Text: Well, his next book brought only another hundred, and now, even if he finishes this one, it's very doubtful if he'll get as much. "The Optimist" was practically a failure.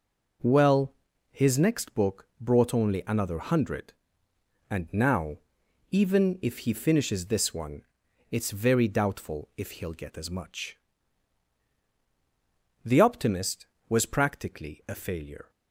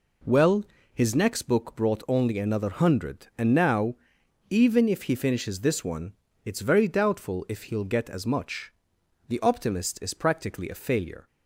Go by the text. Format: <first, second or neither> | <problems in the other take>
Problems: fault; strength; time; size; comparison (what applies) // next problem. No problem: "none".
first | says "is" for "was"; at 10.0 s